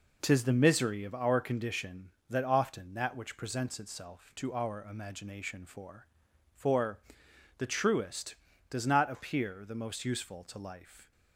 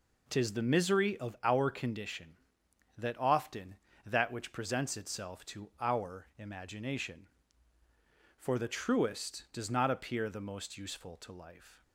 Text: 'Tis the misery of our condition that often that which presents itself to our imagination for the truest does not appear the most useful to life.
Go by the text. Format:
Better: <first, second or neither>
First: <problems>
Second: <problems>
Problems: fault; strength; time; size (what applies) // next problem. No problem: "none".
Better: second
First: says "for" twice; at 6.5 s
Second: none